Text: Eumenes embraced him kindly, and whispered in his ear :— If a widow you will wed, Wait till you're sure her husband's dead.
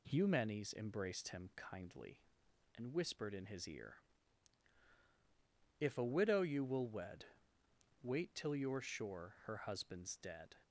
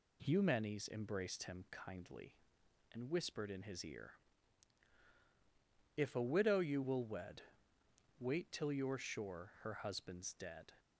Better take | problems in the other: neither | none

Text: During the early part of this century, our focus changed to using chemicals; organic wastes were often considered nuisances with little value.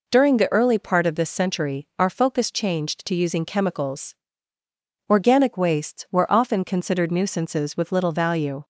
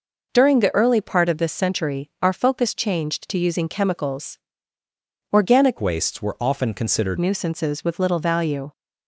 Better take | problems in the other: first | changes voice from "wastes" to "considered"; from 5.8 to 7.1 s; 1.3 s long

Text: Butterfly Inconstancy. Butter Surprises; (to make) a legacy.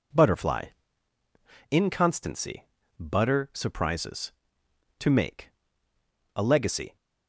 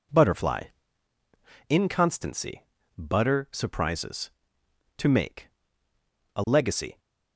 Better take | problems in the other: neither | pauses between "Butterfly" and "Inconstancy"; the same in both

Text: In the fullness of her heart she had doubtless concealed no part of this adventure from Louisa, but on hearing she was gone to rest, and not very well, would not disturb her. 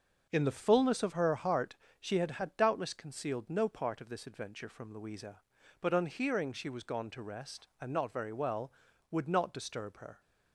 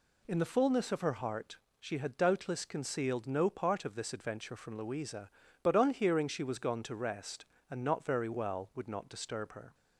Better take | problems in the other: second | starts louder than the rest; noticeable; until 1.3 s; 6 dB // pauses between "heart" and "she"; slight; at 1.7 s; 0.24 s long; slight in the second // says "had" twice; at 2.3 s

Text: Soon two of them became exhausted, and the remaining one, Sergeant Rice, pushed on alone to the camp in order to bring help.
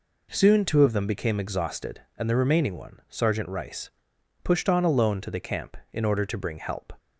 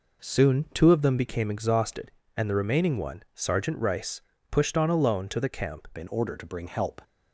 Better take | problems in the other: first | changes voice at "in"; from 5.9 s on; 1.1 s long

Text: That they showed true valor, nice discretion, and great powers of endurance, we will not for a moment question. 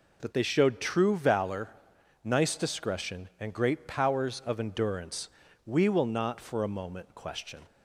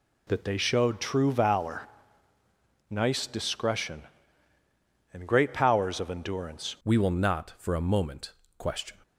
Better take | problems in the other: first | changes voice at "we"; from 6.8 s on; 2.2 s long // pauses between "moment" and "question"; slight; at 8.3 s; 0.24 s long

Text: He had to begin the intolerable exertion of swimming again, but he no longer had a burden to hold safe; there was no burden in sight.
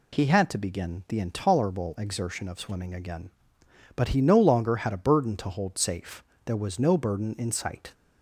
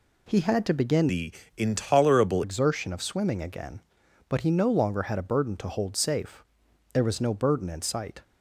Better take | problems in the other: first | changes voice from "the" to "intolerable"; from 1.0 to 2.4 s; 1.4 s long // pauses between "the" and "intolerable"; slight; at 1.3 s; 0.24 s long

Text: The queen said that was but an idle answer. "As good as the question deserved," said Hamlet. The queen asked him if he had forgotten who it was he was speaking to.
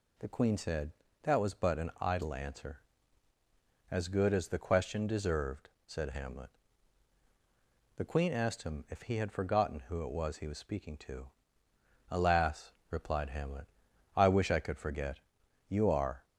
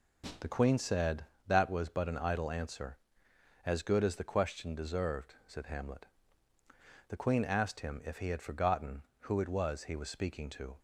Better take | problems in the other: second | goes on to say "Alas replied Hamlet I wish I could forget You are"; strong; from 12.0 s on; 4.1 s long

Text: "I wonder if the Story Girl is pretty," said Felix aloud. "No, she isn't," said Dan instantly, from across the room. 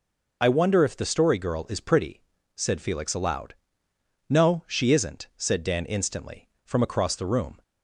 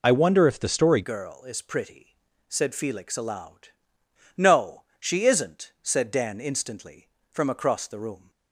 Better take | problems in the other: first | changes voice at "Girl"; from 1.0 s on; 7.3 s long

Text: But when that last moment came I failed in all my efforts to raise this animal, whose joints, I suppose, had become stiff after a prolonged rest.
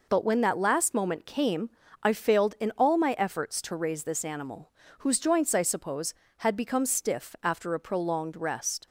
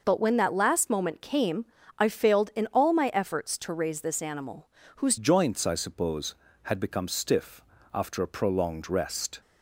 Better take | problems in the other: first | pauses between "came" and "I"; slight; at 1.6 s; 0.34 s long; slight in the first // changes voice at "joints"; from 5.1 s on; 4.3 s long // pauses between "stiff" and "after"; slight; at 7.6 s; 0.32 s long

